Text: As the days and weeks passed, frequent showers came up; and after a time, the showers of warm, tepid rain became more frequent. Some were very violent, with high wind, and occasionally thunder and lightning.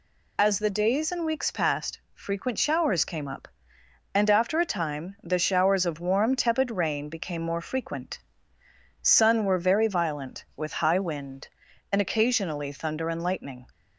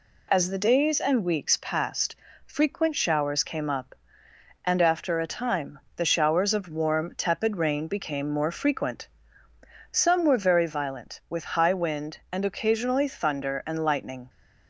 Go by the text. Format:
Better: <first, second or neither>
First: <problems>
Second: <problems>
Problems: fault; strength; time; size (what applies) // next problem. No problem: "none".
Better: second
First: says "Sun" for "Some"; at 9.0 s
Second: none